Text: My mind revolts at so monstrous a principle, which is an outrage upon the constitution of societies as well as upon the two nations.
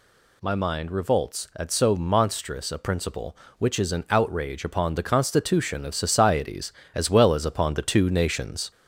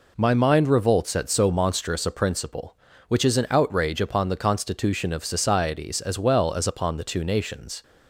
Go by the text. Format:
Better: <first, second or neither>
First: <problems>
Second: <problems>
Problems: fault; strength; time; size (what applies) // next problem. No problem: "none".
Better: second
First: gets louder; slight; throughout; 3 dB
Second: none